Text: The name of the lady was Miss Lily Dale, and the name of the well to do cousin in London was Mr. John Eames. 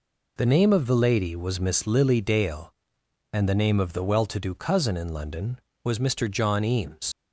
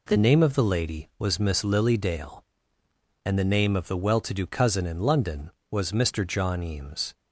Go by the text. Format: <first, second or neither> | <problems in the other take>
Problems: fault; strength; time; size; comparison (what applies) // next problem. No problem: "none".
second | leaves "Eames" unfinished; at 7.1 s; 75 ms